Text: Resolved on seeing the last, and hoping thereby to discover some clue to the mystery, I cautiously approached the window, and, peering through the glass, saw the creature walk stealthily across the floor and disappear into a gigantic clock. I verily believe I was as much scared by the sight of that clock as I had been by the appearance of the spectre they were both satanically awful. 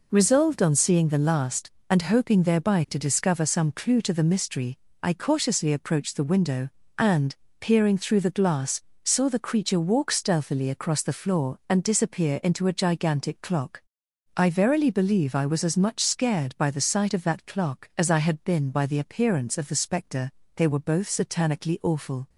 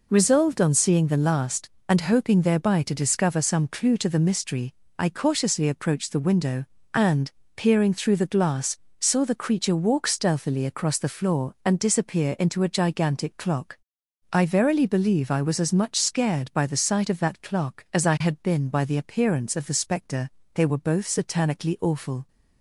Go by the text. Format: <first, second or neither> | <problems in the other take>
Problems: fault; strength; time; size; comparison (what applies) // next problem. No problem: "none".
neither | pauses between "spectre" and "they"; slight; the same in both